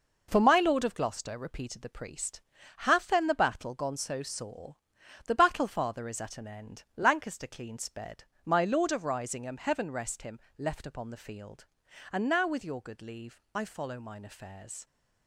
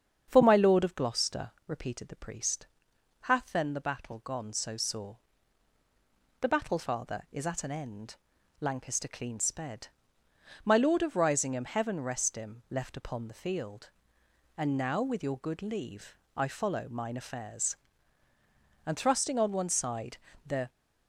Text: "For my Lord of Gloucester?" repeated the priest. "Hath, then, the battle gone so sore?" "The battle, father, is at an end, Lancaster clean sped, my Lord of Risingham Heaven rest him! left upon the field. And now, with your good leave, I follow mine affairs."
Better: first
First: none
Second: starts louder than the rest; strong; until 1.2 s; 7.5 dB // goes on to say "And thrusting on one side the"; strong; from 18.8 s on; 1.8 s long

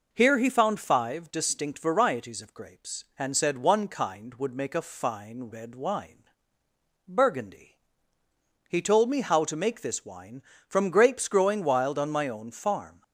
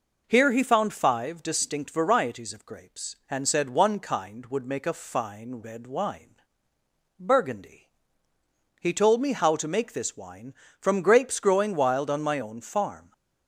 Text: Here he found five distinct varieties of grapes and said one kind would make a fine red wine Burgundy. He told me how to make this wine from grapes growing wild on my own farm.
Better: neither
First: pauses between "wine" and "Burgundy"; noticeable; at 6.1 s; 0.90 s long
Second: pauses between "wine" and "Burgundy"; noticeable; at 6.3 s; 0.90 s long

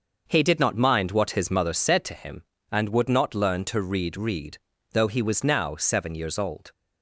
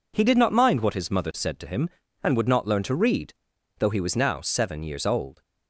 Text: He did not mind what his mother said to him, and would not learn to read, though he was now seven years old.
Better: second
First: starts louder than the rest; until 1.2 s; 6 dB // says "read" twice; at 4.1 s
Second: none

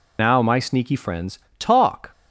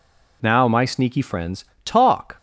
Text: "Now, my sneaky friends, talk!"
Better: second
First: loses the start of "Now"; at 0.1 s; 35 ms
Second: none

